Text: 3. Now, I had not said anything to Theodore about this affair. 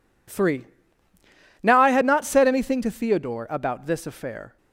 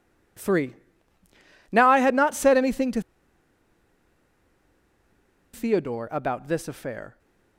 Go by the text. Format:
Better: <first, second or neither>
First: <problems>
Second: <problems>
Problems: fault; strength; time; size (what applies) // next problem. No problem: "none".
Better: first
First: none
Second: pauses between "to" and "Theodore"; strong; at 3.0 s; 2.5 s long